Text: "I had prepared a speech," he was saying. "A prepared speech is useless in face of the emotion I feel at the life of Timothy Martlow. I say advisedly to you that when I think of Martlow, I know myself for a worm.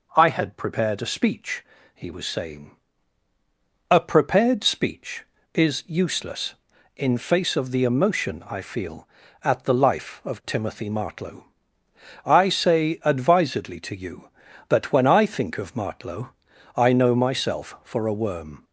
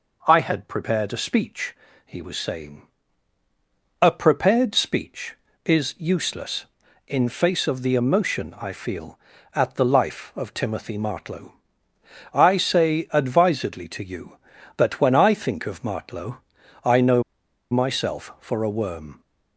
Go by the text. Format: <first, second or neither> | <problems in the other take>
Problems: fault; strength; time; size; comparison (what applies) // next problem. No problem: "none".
first | pauses between "know" and "myself"; noticeable; at 17.2 s; 0.48 s long